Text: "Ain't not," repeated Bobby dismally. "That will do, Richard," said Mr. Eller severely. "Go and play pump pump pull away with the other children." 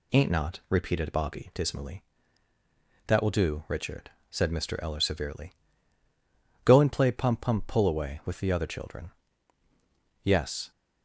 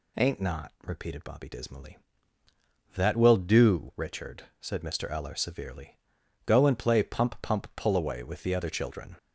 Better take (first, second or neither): second